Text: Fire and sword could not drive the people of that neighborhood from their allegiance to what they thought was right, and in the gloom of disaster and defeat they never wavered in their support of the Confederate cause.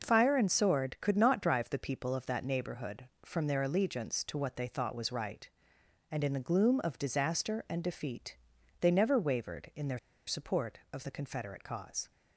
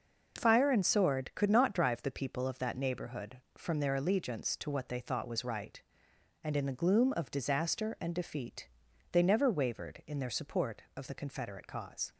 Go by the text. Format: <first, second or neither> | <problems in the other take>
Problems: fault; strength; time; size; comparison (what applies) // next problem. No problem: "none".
second | pauses between "defeat" and "they"; noticeable; at 8.3 s; 0.46 s long; noticeable in the second // pauses between "their" and "support"; slight; at 9.9 s; 0.28 s long